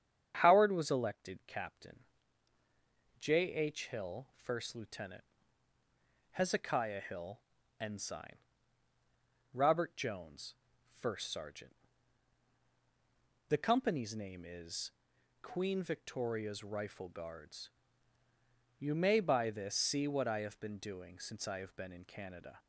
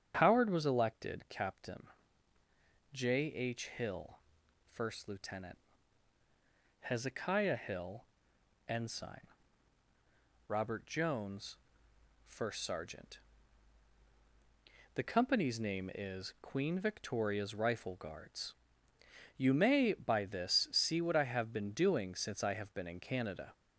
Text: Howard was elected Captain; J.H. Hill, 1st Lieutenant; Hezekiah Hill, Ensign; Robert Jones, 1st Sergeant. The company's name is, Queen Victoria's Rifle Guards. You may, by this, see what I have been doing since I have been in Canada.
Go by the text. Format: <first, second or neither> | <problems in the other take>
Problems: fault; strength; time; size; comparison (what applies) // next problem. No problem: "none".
neither | starts louder than the rest; strong; the same in both